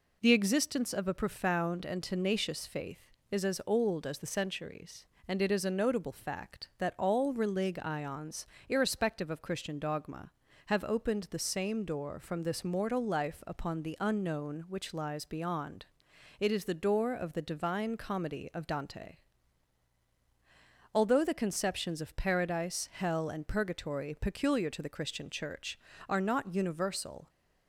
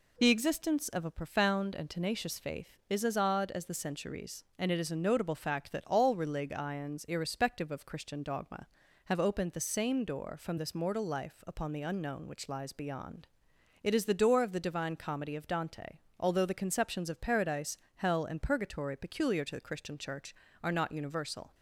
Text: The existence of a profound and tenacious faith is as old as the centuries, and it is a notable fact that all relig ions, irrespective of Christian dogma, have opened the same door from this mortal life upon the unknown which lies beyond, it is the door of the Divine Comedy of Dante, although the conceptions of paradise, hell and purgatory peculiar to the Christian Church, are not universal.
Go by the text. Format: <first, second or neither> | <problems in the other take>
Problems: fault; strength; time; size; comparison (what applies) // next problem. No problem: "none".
first | says "odd" for "old"; at 3.1 s